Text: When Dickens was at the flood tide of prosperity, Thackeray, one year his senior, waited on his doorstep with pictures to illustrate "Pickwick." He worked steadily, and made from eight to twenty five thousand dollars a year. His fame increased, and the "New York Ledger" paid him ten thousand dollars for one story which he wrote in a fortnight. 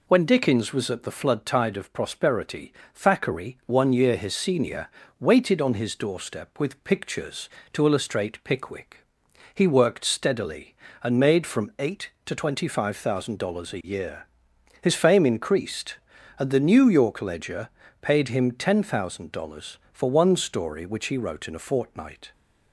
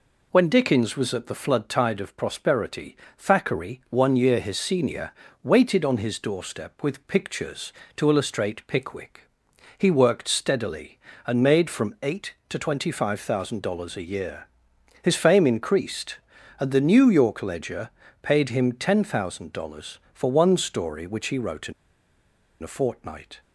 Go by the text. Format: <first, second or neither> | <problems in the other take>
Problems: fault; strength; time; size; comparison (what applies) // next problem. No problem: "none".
first | pauses between "Ledger" and "paid"; slight; at 17.9 s; 0.32 s long; slight in the first // pauses between "in" and "a"; noticeable; at 21.7 s; 0.89 s long